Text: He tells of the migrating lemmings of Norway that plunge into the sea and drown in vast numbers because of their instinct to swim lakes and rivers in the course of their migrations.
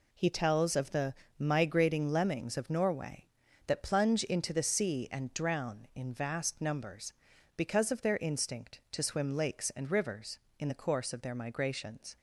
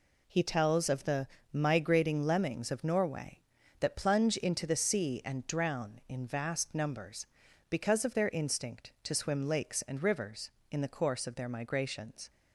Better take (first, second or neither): neither